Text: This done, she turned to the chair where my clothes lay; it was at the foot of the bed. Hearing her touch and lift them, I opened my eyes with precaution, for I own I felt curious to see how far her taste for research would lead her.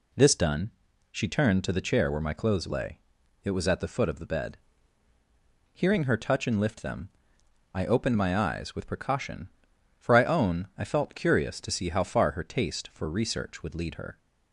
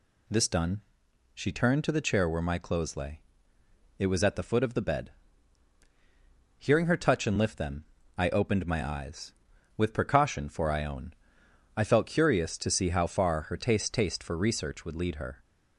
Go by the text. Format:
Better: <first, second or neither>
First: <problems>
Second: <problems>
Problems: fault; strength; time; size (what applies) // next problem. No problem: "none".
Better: first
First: none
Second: pauses between "own" and "I"; noticeable; at 11.1 s; 0.62 s long // says "taste" twice; at 13.9 s